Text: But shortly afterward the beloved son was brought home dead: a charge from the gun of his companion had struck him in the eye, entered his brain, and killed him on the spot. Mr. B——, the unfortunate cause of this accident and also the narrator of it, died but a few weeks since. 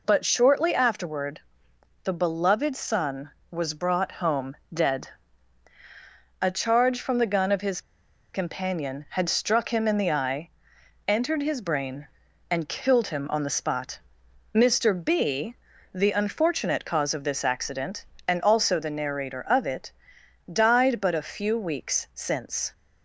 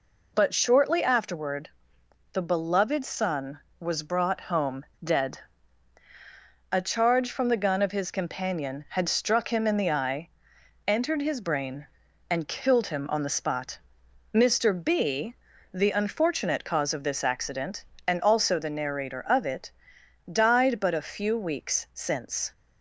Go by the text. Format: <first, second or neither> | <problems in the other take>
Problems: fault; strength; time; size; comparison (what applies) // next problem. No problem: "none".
second | pauses between "afterward" and "the"; noticeable; at 1.3 s; 0.64 s long; noticeable in the second // pauses between "home" and "dead"; slight; at 4.5 s; 0.16 s long; slight in the second // pauses between "his" and "companion"; noticeable; at 7.8 s; 0.52 s long